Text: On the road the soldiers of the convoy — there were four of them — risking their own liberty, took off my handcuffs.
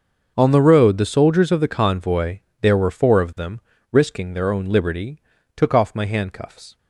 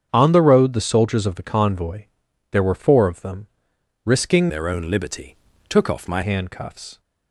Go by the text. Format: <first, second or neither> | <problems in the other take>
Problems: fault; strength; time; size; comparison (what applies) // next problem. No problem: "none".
first | starts louder than the rest; strong; until 1.1 s; 8 dB; noticeable in the first // changes voice from "their" to "my"; from 4.4 to 6.2 s; 1.8 s long